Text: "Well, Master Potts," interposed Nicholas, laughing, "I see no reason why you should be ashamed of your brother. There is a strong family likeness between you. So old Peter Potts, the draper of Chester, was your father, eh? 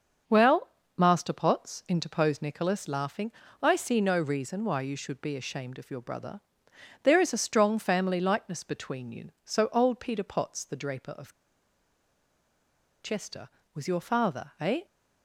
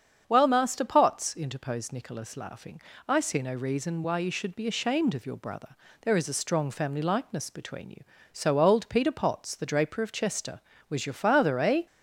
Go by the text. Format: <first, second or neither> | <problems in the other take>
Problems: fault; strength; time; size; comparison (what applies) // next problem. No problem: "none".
second | starts louder than the rest; until 1.5 s; 6.5 dB; strong in the second // pauses between "of" and "Chester"; strong; at 11.3 s; 1.7 s long